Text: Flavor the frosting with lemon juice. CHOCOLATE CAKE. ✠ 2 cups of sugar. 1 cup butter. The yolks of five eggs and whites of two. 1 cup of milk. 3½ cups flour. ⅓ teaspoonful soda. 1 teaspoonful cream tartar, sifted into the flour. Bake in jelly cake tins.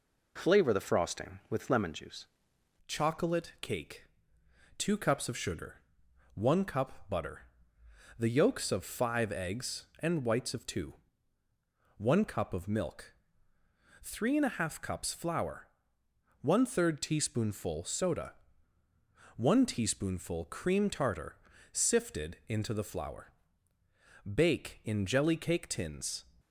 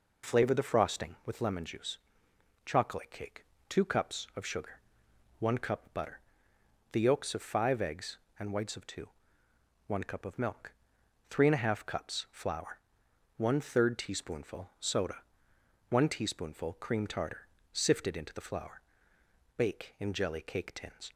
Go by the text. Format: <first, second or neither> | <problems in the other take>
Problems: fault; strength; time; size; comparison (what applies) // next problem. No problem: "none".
second | changes voice at "CHOCOLATE"; from 2.8 s on; 23.4 s long